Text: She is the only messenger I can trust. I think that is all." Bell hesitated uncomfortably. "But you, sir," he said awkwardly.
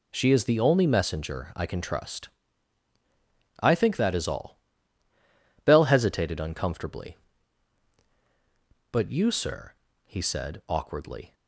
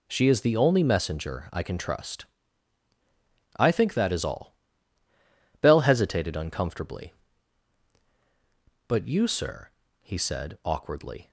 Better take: neither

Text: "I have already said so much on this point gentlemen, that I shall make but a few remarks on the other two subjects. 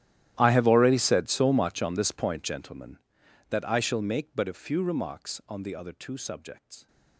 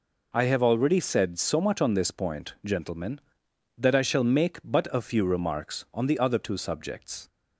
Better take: second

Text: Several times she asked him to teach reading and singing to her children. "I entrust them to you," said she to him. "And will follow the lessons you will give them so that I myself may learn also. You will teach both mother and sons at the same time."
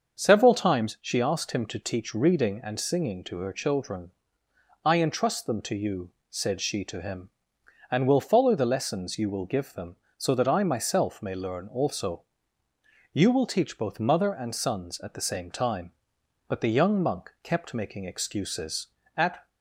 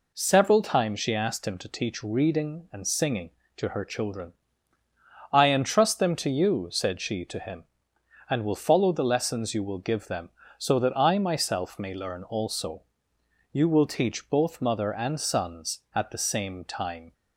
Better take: second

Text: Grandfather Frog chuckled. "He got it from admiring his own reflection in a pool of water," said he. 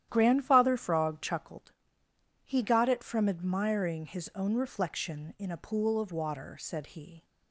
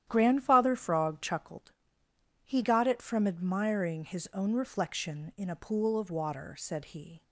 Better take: neither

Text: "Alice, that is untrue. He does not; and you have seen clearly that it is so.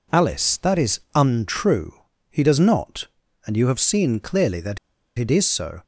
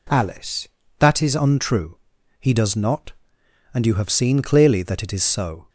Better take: second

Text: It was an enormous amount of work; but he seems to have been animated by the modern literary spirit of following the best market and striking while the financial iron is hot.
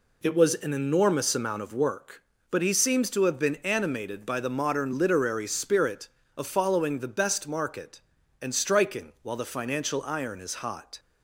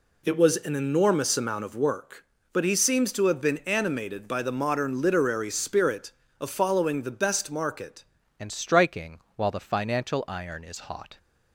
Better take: first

